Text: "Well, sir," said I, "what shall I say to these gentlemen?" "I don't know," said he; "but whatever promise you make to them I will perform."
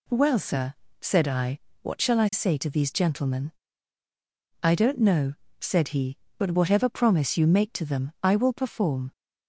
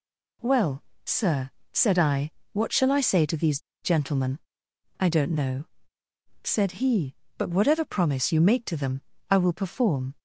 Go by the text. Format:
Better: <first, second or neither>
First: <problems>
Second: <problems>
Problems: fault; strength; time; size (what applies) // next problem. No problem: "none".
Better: first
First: none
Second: pauses between "these" and "gentlemen"; slight; at 3.5 s; 0.23 s long // pauses between "them" and "I"; slight; at 9.0 s; 0.30 s long